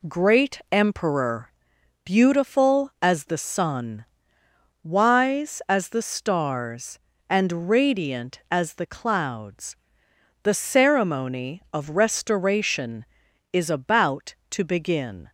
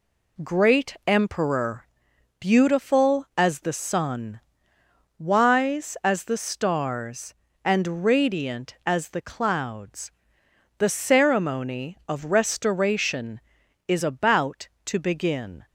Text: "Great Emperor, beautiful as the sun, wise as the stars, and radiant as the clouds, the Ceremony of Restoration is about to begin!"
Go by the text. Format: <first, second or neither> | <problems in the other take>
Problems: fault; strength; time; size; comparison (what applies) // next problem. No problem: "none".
neither | none